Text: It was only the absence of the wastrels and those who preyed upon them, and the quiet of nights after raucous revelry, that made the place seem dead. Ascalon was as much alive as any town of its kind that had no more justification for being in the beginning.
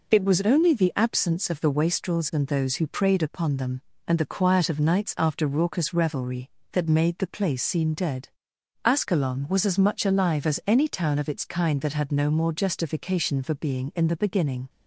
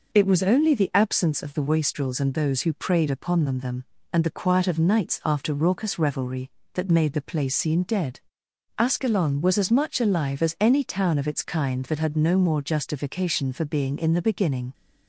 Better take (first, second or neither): first